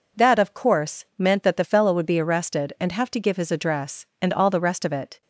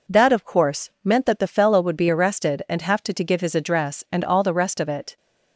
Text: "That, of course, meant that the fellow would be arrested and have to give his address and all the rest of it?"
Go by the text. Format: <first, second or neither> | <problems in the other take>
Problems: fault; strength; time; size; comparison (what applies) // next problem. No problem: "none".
first | says "to" twice; at 3.1 s